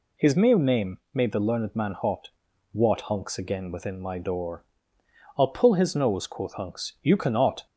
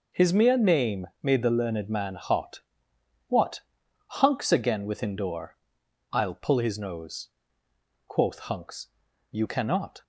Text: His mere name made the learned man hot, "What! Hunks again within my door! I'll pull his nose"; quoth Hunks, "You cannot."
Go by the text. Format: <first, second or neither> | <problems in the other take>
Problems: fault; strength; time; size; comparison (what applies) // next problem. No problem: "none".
first | pauses between "name" and "made"; slight; at 1.0 s; 0.15 s long; slight in the first // skips "my"; at 5.1 s